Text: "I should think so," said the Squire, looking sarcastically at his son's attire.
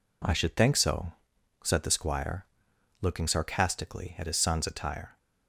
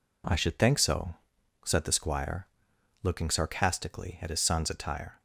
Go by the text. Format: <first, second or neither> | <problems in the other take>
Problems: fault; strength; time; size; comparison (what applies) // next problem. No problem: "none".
neither | none